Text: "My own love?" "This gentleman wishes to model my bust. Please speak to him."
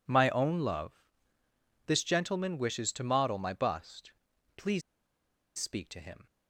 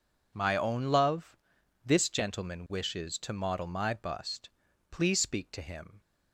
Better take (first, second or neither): second